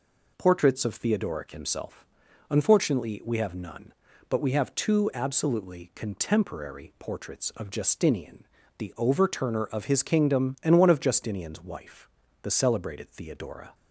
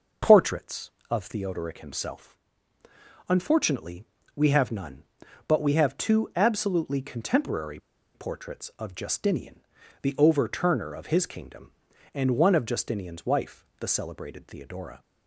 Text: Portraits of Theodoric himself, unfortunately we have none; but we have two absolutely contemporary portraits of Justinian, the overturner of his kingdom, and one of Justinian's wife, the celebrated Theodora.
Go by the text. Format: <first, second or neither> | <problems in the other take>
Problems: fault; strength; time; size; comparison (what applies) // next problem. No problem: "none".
first | starts louder than the rest; noticeable; until 1.4 s; 6 dB // pauses between "unfortunately" and "we"; slight; at 4.0 s; 0.30 s long // pauses between "contemporary" and "portraits"; at 7.7 s; 0.36 s long